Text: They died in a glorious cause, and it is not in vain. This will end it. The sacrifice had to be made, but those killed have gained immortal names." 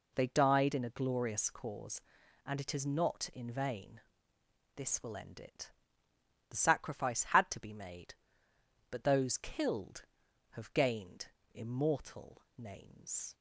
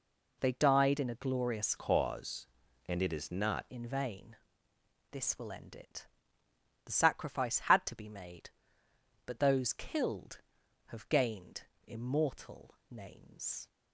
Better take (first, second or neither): first